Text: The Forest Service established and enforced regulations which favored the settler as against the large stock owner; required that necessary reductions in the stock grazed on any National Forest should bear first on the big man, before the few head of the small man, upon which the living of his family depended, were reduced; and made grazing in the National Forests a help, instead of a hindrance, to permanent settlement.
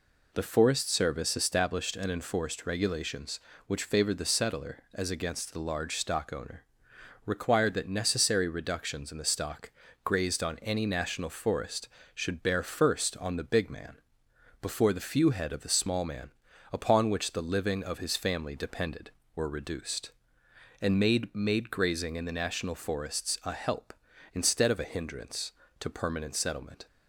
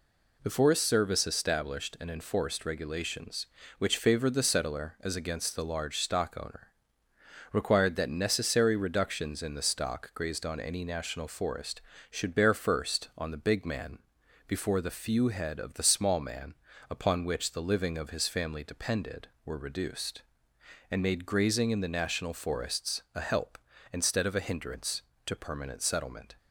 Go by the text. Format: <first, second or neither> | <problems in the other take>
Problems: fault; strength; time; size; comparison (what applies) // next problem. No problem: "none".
second | pauses between "stock" and "grazed"; slight; at 9.7 s; 0.32 s long // says "made" twice; at 21.3 s